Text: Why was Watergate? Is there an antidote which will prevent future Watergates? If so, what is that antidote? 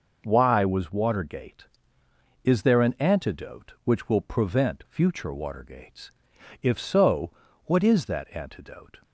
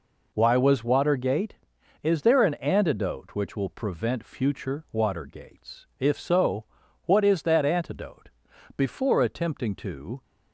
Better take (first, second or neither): first